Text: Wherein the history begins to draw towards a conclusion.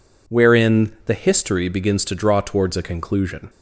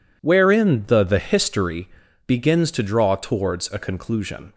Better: first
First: none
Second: says "the" twice; at 1.0 s // pauses between "history" and "begins"; at 1.8 s; 0.36 s long

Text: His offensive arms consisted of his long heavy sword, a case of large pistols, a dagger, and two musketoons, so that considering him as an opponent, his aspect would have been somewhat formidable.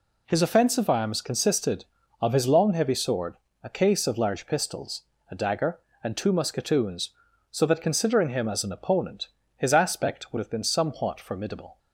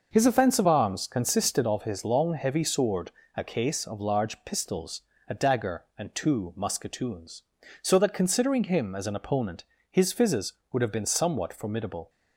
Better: first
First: none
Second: says "fizzes" for "aspect"; at 10.1 s

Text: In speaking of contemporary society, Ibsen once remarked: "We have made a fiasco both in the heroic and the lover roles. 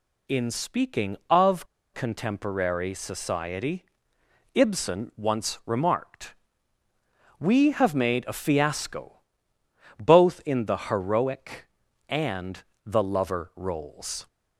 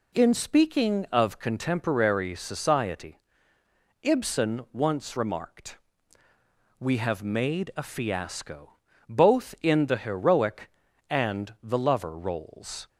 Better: second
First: pauses between "of" and "contemporary"; slight; at 1.6 s; 0.27 s long // pauses between "fiasco" and "both"; noticeable; at 9.2 s; 0.76 s long // pauses between "and" and "the"; slight; at 12.6 s; 0.20 s long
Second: pauses between "fiasco" and "both"; slight; at 8.7 s; 0.34 s long

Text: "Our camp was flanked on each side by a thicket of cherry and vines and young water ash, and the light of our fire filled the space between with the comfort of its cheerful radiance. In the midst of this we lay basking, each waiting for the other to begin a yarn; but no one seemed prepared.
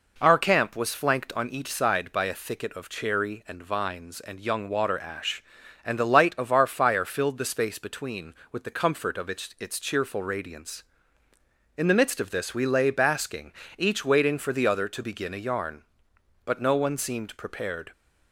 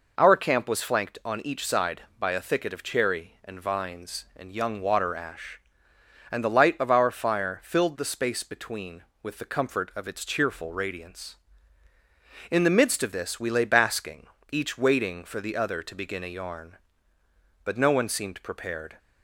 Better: second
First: says "its" twice; at 9.5 s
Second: none

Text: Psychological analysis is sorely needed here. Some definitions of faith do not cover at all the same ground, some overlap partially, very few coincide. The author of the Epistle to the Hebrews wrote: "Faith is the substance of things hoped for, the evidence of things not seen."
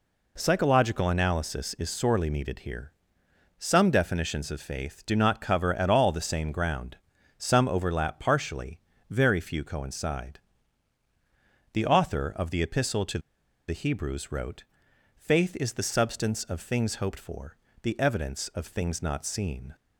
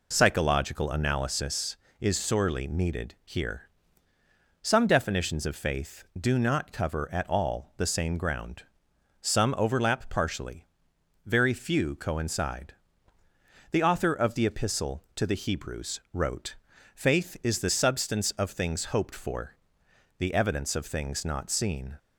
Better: second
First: pauses between "to" and "the"; noticeable; at 13.1 s; 0.49 s long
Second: none

